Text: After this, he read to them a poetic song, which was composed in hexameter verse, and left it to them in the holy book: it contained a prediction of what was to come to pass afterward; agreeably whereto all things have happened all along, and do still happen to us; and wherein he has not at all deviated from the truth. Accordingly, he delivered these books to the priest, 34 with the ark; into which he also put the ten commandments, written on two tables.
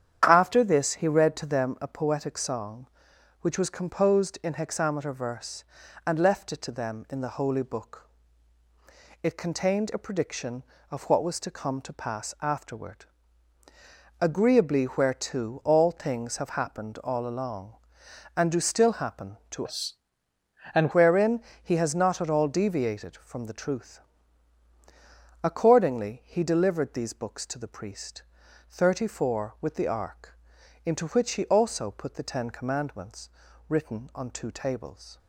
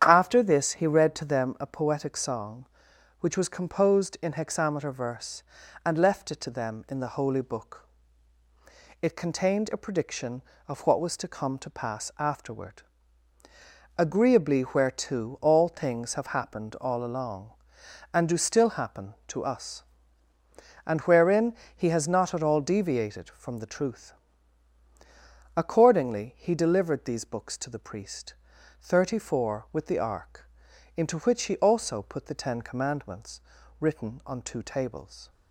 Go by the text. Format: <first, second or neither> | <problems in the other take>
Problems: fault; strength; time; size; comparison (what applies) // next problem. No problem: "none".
second | starts louder than the rest; strong; until 1.2 s; 9 dB; strong in the second // changes voice from "us" to "and"; from 19.6 to 20.9 s; 1.3 s long // pauses between "wherein" and "he"; slight; at 21.3 s; 0.24 s long; slight in the second